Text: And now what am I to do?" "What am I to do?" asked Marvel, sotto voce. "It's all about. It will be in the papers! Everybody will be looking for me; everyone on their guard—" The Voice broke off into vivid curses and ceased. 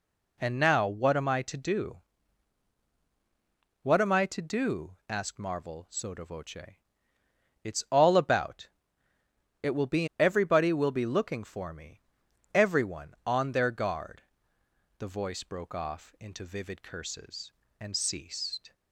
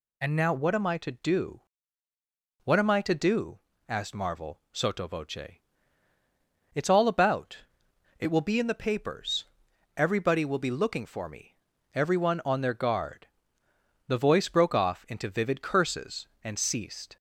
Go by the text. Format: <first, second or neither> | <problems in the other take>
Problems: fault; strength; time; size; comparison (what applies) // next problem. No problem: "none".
second | skips "in the papers"; at 10.1 s